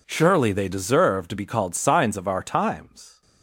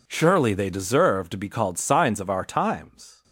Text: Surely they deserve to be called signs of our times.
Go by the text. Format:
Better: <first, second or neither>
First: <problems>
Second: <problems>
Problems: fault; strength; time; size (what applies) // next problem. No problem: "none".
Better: neither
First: none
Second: none